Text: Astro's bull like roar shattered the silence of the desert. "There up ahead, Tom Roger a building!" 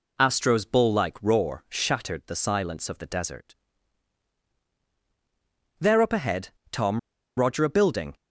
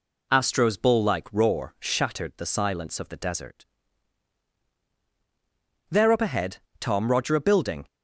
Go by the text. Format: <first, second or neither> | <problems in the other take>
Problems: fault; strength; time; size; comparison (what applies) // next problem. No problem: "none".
second | pauses between "Tom" and "Roger"; at 6.9 s; 0.40 s long